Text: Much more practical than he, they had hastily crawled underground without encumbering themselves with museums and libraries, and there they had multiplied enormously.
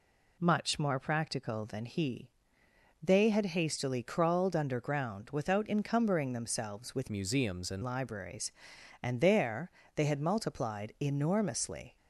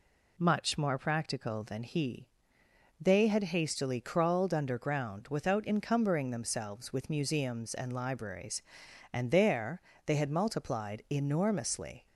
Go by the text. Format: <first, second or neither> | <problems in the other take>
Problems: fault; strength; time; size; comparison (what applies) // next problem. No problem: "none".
second | changes voice from "museums" to "and"; from 7.0 to 7.8 s; 0.8 s long // pauses between "there" and "they"; slight; at 9.7 s; 0.24 s long; slight in the second